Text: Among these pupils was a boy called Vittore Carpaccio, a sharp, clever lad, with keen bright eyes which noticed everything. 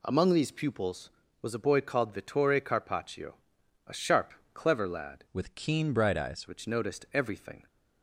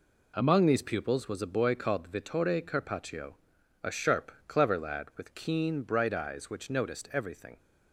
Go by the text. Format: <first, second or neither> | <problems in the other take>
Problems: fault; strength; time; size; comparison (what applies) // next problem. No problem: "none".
second | changes voice from "with" to "eyes"; from 5.3 to 6.4 s; 1.1 s long